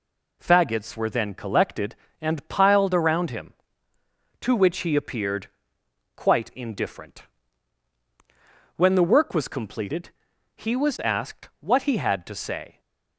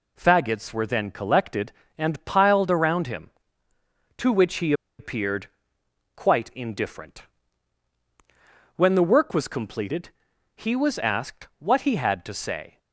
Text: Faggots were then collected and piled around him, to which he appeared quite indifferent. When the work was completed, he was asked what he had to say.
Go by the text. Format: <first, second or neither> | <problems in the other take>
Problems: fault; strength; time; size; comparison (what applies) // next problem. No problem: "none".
first | pauses between "he" and "appeared"; slight; at 4.7 s; 0.26 s long // pauses between "appeared" and "quite"; noticeable; at 5.4 s; 0.66 s long; noticeable in the first